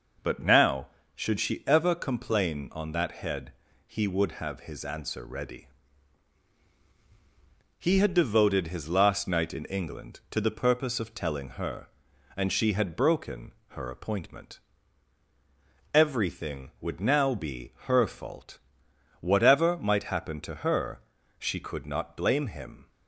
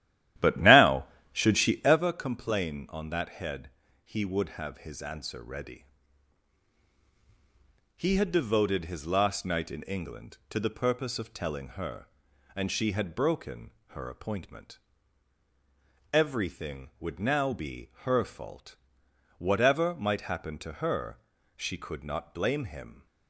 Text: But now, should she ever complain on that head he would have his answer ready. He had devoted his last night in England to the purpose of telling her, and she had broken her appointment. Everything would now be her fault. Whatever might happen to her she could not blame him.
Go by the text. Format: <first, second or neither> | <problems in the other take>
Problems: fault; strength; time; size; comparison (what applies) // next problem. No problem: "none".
first | starts louder than the rest; strong; until 2.0 s; 13 dB // pauses between "head" and "he"; slight; at 3.6 s; 0.34 s long; slight in the first // pauses between "broken" and "her"; slight; at 13.7 s; 0.16 s long; slight in the first // pauses between "her" and "she"; at 21.1 s; 0.38 s long; also in the first